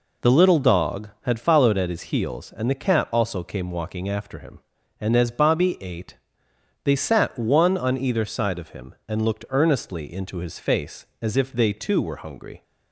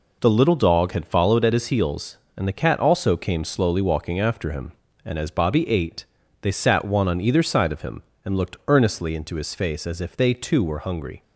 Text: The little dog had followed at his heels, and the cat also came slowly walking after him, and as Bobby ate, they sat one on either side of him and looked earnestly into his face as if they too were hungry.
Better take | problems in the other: second | skips "slowly"; at 3.7 s

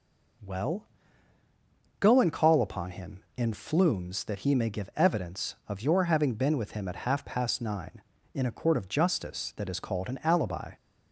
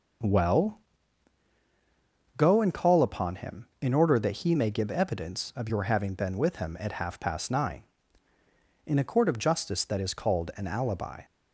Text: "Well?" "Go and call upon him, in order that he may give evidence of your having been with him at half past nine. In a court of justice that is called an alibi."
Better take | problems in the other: second | says "flumes" for "order"; at 3.5 s

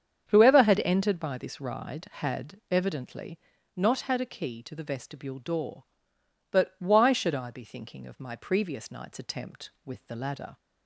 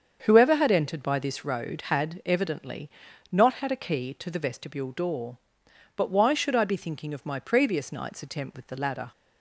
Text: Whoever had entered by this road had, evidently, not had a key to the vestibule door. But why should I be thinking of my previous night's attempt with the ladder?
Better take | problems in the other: second | starts louder than the rest; strong; until 1.2 s; 7.5 dB; also in the second // says "ride" for "road"; at 1.6 s

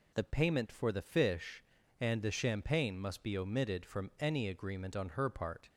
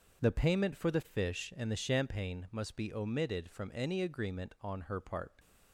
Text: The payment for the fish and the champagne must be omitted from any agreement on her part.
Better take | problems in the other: neither | none

